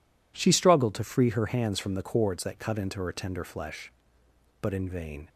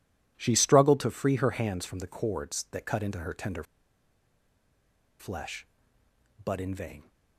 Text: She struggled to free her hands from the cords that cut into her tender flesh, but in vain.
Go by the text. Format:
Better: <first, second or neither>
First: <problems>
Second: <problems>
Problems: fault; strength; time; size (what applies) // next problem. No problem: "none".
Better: first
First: none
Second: pauses between "tender" and "flesh"; strong; at 3.6 s; 1.5 s long